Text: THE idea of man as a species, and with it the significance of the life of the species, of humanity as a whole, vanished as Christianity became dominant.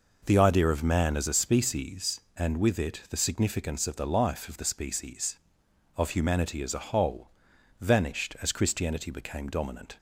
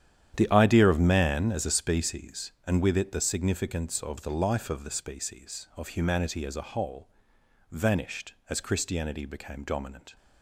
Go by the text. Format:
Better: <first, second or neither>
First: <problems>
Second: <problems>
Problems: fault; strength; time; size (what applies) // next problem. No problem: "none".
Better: first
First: none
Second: gets quieter; strong; throughout; 12.5 dB